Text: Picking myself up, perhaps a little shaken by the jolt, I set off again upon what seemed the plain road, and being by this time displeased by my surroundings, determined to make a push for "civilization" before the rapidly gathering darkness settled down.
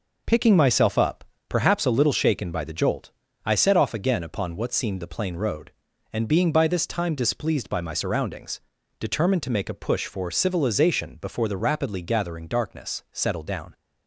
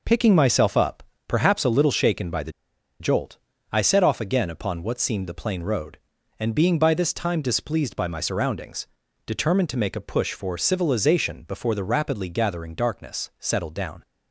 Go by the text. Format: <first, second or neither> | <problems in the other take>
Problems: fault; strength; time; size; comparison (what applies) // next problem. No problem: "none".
first | pauses between "the" and "jolt"; noticeable; at 2.5 s; 0.48 s long